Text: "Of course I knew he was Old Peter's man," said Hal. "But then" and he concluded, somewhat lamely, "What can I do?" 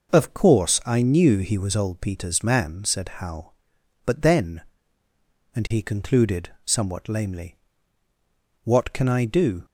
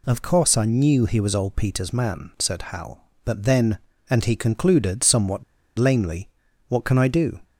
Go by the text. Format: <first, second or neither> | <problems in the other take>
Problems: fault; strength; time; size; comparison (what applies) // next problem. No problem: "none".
first | pauses between "somewhat" and "lamely"; slight; at 5.4 s; 0.35 s long